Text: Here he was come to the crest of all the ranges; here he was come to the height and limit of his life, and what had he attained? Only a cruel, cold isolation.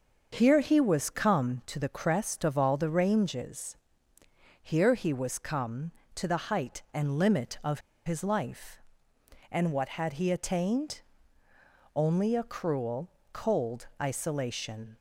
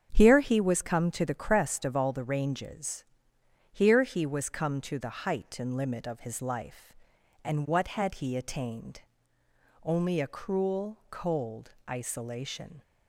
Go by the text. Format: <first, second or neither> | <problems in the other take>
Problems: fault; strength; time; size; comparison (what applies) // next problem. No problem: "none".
second | starts louder than the rest; until 1.4 s; 6.5 dB; strong in the second // pauses between "of" and "his"; slight; at 7.8 s; 0.25 s long // pauses between "cold" and "isolation"; slight; at 13.8 s; 0.16 s long